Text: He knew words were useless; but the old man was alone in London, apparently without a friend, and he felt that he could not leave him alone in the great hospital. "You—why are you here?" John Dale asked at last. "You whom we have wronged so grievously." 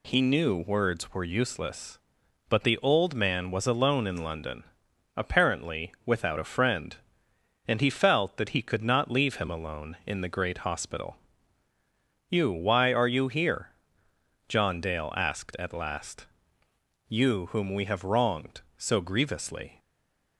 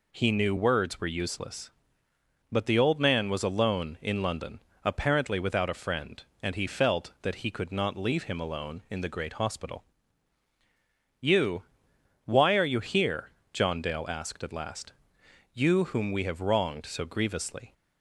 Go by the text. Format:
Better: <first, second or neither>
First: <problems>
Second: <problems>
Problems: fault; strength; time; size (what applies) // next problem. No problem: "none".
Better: second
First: stays silent after the last word; slight; from 19.7 s on; 0.6 s long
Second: none